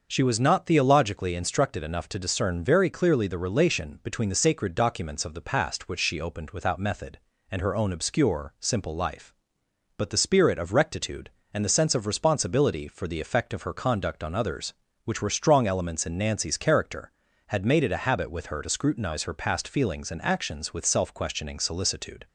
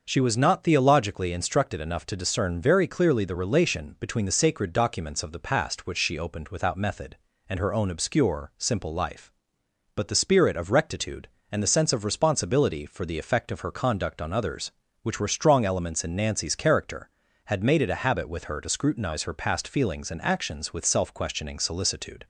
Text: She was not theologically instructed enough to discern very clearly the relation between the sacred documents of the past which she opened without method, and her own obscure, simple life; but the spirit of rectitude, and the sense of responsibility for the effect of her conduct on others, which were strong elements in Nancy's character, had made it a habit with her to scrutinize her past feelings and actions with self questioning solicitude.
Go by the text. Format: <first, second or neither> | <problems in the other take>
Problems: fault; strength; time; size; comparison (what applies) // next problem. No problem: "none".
neither | starts louder than the rest; the same in both